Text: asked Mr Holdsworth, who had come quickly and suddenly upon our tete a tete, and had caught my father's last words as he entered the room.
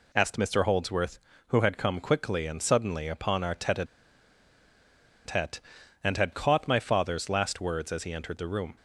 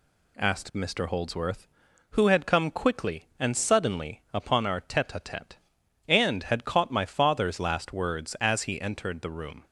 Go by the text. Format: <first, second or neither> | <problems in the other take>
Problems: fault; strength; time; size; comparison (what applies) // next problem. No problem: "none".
second | pauses between "a" and "tete"; strong; at 3.8 s; 1.4 s long